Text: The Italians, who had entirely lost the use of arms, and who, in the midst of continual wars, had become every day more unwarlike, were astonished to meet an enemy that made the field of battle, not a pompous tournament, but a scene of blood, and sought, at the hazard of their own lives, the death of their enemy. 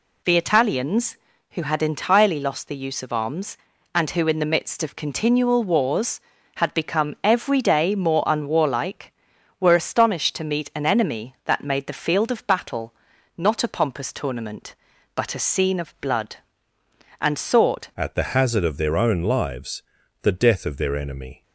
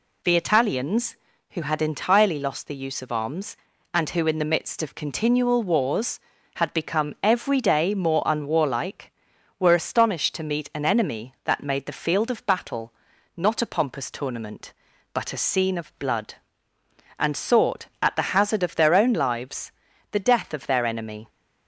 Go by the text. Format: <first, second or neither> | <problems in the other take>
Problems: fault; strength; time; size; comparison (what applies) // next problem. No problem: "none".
second | changes voice at "at"; from 17.9 s on; 3.5 s long